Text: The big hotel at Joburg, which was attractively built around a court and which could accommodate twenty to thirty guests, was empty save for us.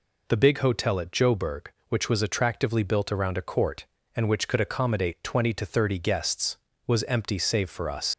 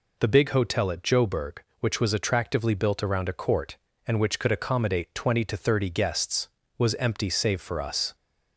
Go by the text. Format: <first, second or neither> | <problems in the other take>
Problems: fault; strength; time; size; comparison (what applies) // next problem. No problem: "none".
second | leaves "us" unfinished; at 8.1 s; 100 ms